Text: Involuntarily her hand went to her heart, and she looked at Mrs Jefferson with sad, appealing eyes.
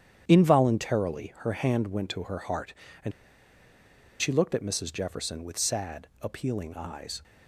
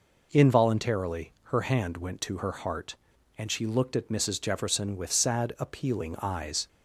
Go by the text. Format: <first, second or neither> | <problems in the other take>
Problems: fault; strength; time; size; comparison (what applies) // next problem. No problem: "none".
second | starts louder than the rest; strong; until 1.2 s; 9 dB // pauses between "and" and "she"; at 3.1 s; 1.0 s long